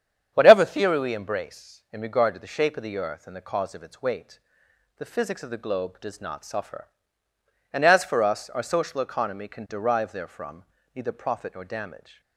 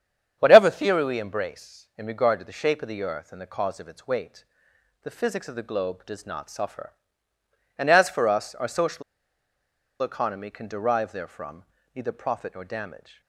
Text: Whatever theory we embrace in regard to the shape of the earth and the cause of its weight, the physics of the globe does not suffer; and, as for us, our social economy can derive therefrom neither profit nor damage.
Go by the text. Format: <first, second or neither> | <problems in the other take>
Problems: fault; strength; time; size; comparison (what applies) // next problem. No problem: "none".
first | starts louder than the rest; strong; until 1.3 s; 9 dB; strong in the first // pauses between "social" and "economy"; at 9.0 s; 0.99 s long // pauses between "therefrom" and "neither"; slight; at 11.6 s; 0.30 s long; slight in the first